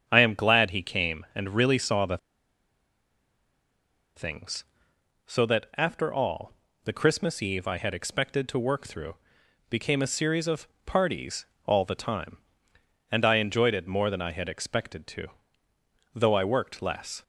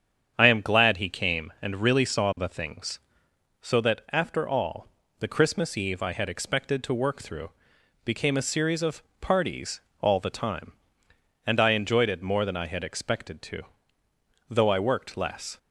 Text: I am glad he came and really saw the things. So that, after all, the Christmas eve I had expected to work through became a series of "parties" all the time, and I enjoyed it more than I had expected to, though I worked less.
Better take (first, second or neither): second